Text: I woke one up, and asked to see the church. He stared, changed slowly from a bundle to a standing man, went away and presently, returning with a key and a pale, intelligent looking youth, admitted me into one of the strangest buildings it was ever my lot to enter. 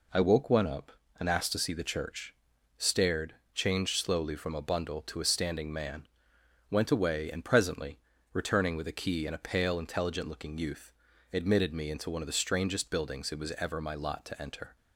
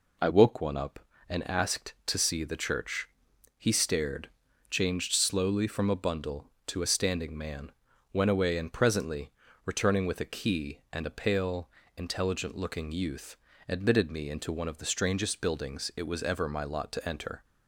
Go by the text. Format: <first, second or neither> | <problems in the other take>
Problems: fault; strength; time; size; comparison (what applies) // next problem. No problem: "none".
second | skips "He"; at 2.5 s